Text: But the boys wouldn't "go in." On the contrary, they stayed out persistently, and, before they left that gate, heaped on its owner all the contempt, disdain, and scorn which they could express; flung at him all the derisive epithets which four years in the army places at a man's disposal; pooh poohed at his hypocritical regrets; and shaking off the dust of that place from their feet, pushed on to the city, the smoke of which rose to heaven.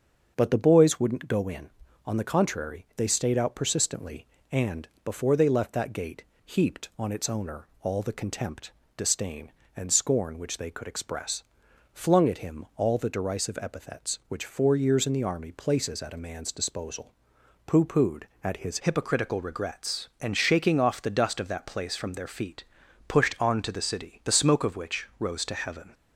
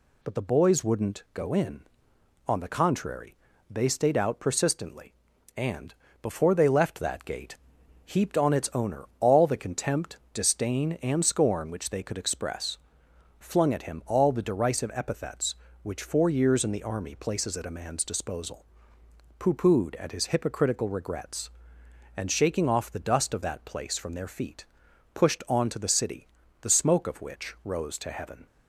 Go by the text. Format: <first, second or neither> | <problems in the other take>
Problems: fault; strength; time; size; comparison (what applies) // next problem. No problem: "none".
second | starts louder than the rest; until 1.3 s; 7 dB // changes voice at "hypocritical"; from 18.7 s on; 7.2 s long